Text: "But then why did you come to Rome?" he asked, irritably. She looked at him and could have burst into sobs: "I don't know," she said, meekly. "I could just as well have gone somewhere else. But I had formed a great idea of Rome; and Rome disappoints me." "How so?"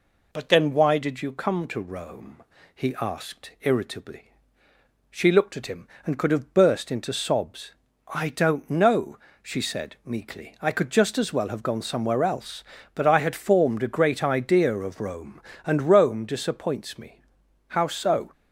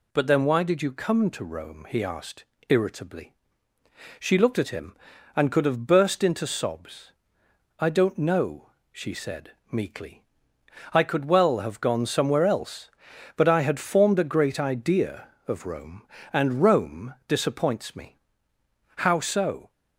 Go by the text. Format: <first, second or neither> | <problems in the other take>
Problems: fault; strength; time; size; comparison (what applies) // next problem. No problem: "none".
first | skips "just as"; at 11.2 s